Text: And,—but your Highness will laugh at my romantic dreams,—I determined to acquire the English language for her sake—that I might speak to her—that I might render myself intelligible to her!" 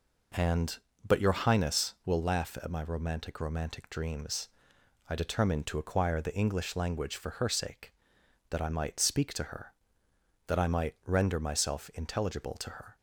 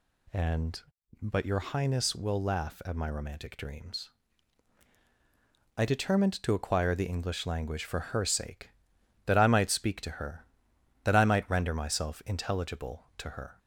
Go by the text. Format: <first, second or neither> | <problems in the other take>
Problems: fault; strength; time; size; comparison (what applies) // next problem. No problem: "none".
second | says "romantic" twice; at 3.3 s